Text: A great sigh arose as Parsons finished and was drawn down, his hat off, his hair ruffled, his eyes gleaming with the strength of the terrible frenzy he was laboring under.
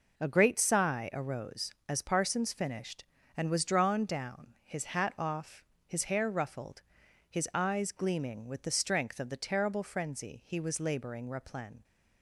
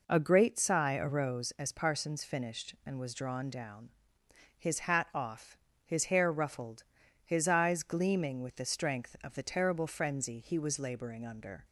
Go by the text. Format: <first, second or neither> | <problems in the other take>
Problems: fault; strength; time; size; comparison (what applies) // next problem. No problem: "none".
second | says "replen" for "under"; at 11.2 s